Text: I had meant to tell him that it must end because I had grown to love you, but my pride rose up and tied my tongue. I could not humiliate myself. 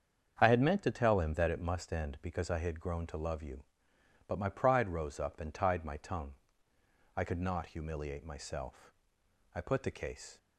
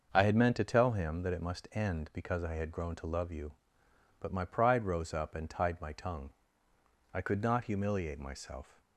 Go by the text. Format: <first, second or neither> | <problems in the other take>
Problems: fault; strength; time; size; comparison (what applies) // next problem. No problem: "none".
second | starts louder than the rest; strong; until 1.4 s; 7.5 dB; also in the second // goes on to say "I put the case"; noticeable; from 9.5 s on; 0.82 s long